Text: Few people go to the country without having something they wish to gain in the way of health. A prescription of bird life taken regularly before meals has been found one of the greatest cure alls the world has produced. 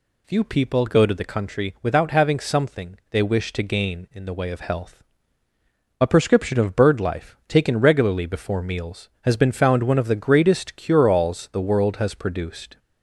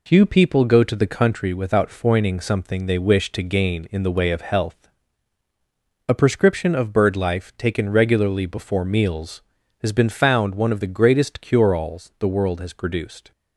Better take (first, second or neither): first